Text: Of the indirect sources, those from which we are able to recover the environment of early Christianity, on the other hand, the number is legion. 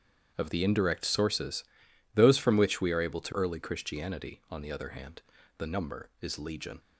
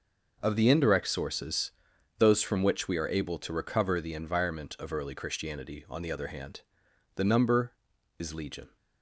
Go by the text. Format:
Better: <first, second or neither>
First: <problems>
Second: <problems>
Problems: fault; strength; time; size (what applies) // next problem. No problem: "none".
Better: second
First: starts louder than the rest; strong; until 1.3 s; 9 dB // skips "recover the environment of"; at 3.3 s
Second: none